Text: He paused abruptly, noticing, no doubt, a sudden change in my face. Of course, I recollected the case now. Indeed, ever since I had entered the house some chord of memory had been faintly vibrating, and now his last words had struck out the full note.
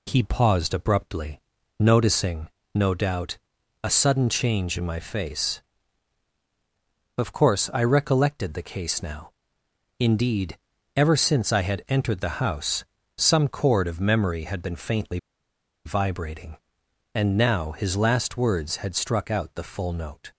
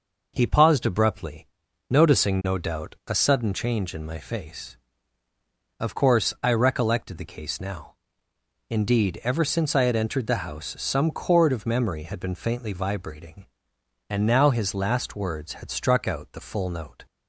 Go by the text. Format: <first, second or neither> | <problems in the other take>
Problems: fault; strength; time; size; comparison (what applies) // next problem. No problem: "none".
second | pauses between "house" and "some"; slight; at 12.8 s; 0.32 s long // pauses between "faintly" and "vibrating"; noticeable; at 15.1 s; 0.67 s long